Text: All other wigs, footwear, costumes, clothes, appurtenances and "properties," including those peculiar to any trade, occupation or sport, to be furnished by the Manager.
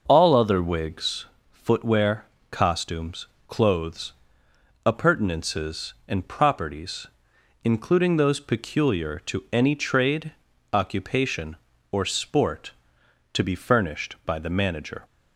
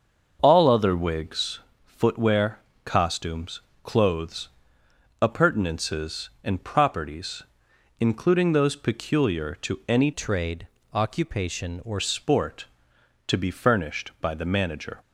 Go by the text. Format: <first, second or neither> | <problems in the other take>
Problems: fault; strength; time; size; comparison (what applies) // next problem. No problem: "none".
first | starts louder than the rest; until 1.4 s; 6.5 dB; noticeable in the first // changes voice from "trade" to "or"; from 10.1 to 11.9 s; 1.8 s long